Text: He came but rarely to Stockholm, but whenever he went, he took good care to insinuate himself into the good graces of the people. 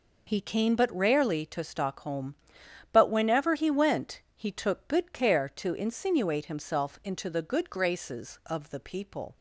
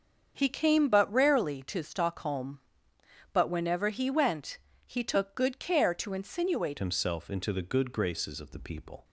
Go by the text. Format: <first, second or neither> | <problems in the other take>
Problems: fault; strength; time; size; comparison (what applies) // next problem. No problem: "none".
first | starts louder than the rest; until 1.3 s; 7 dB // changes voice at "himself"; from 6.7 s on; 2.3 s long